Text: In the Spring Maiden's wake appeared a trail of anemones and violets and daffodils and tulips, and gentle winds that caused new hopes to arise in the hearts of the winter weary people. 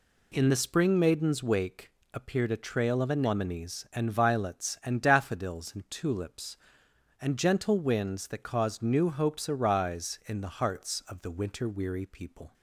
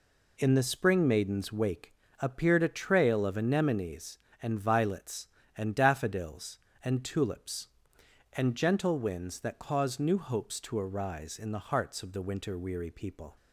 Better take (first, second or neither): second